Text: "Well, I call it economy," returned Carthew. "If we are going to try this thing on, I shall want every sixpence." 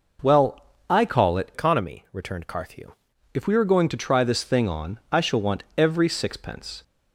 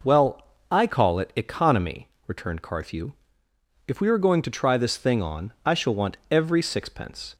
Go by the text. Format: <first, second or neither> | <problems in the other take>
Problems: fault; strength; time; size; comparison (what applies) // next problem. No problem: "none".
second | changes voice from "economy" to "Carthew"; from 1.5 to 2.9 s; 1.4 s long